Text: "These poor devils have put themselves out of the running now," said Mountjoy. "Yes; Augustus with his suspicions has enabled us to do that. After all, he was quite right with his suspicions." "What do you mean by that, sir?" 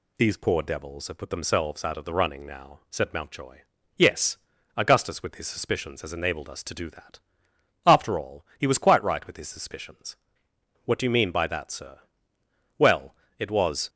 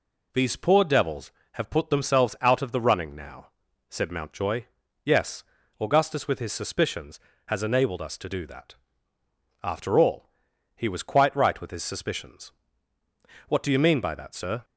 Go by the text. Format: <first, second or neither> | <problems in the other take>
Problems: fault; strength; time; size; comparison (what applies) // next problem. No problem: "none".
second | goes on to say "Well it was"; noticeable; from 12.7 s on; 1.1 s long